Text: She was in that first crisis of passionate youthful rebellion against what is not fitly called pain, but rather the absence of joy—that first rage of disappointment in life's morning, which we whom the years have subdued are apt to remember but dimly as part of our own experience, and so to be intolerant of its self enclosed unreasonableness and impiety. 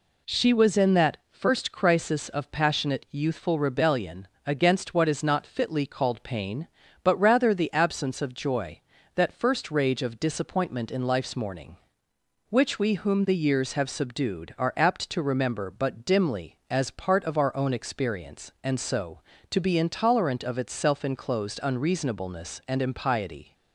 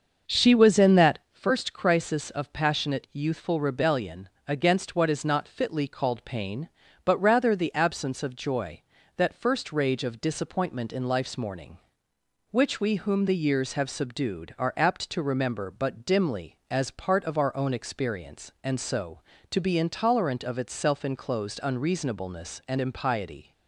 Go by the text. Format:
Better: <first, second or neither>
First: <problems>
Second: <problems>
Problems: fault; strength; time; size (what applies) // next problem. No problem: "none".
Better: first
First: pauses between "rebellion" and "against"; slight; at 4.2 s; 0.16 s long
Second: starts louder than the rest; until 1.3 s; 6.5 dB // pauses between "rebellion" and "against"; slight; at 4.2 s; 0.16 s long